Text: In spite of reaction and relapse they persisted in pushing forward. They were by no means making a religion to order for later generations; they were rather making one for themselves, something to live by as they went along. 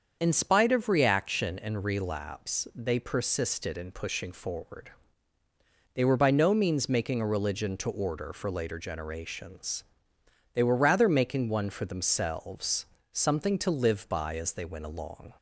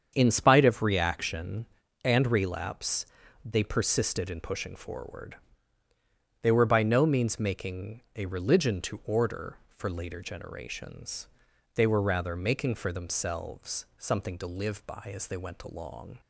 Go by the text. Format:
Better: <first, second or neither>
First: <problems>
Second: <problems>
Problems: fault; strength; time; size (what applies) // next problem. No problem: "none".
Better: first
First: starts louder than the rest; until 1.2 s; 7 dB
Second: starts louder than the rest; strong; until 1.1 s; 7.5 dB // pauses between "relapse" and "they"; at 3.0 s; 0.40 s long // skips "one"; at 12.7 s